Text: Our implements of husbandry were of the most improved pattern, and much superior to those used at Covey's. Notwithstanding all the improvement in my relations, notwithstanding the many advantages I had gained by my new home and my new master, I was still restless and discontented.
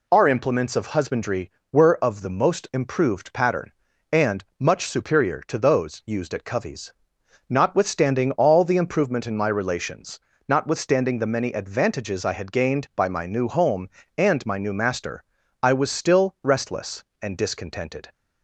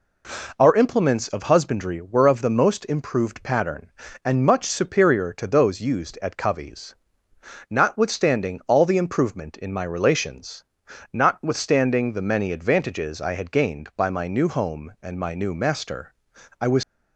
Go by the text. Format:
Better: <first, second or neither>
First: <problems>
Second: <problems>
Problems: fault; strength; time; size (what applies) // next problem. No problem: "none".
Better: first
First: none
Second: stops before "still restless and discontented"; at 16.8 s